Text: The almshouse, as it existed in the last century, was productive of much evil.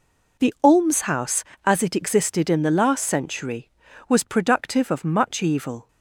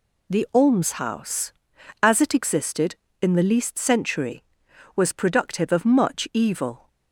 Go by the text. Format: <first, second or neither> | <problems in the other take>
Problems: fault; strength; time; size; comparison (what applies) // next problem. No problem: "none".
first | says "least" for "last"; at 3.4 s